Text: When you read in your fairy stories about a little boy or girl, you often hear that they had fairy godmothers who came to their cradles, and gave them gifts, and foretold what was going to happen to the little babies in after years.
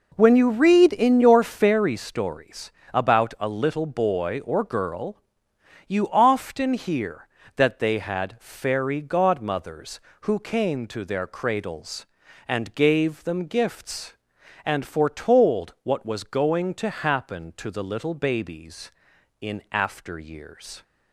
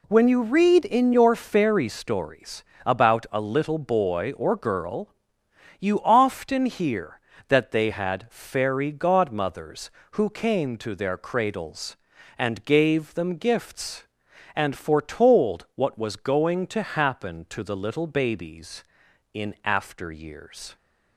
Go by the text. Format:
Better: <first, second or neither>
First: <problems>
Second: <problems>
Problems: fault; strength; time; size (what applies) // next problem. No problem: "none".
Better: second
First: starts louder than the rest; noticeable; until 1.8 s; 4.5 dB // pauses between "stories" and "about"; slight; at 2.7 s; 0.22 s long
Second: pauses between "stories" and "about"; slight; at 2.6 s; 0.22 s long